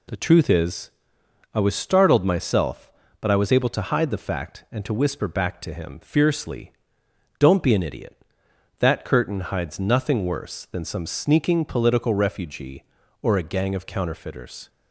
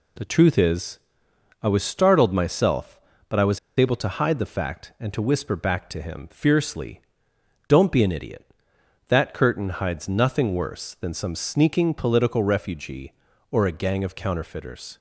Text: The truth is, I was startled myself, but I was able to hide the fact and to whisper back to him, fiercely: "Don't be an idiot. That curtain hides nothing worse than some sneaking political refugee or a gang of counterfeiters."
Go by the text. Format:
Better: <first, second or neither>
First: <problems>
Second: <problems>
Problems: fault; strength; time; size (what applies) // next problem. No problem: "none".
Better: first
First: none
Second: pauses between "was" and "able"; slight; at 3.5 s; 0.18 s long